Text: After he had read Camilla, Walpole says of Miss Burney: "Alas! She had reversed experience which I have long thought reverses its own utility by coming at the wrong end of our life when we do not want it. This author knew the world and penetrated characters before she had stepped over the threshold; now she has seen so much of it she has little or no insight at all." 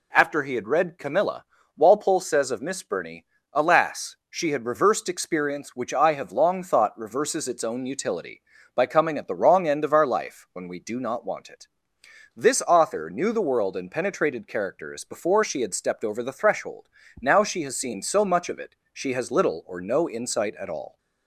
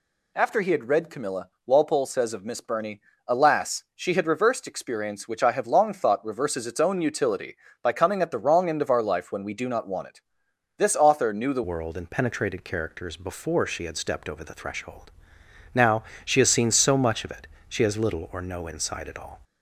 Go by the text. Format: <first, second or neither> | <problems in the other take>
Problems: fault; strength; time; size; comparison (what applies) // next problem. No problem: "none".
first | changes voice at "world"; from 11.6 s on; 7.8 s long // pauses between "now" and "she"; slight; at 16.0 s; 0.24 s long // pauses between "it" and "she"; slight; at 17.4 s; 0.20 s long; slight in the first